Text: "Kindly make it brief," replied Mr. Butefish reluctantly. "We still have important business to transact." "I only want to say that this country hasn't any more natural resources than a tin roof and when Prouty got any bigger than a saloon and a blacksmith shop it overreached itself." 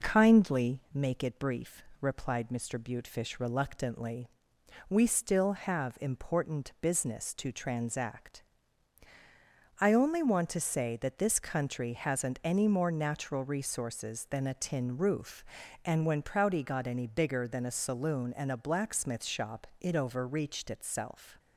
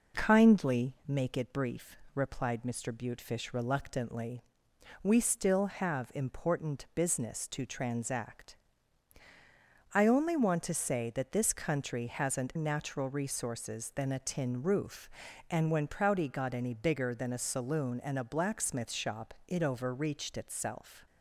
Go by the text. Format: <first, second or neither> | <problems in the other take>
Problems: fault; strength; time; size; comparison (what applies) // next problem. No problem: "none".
first | skips "any more"; at 12.5 s // pauses between "shop" and "it"; slight; at 19.3 s; 0.16 s long; slight in the first